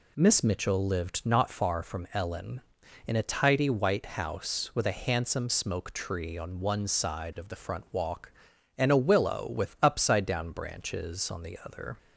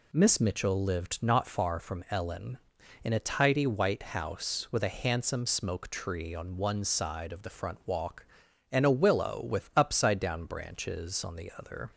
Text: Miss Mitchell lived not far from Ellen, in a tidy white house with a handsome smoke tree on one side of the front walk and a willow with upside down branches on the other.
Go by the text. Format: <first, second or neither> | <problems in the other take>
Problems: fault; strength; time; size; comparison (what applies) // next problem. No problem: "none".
neither | none